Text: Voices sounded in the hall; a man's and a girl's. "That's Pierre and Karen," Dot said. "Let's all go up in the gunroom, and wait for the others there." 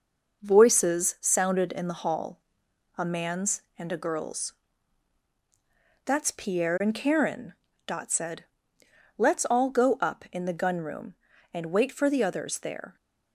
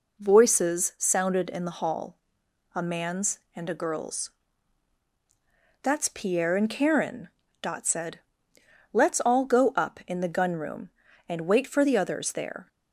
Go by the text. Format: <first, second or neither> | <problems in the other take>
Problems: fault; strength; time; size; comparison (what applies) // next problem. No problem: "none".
second | gets quieter; noticeable; throughout; 5 dB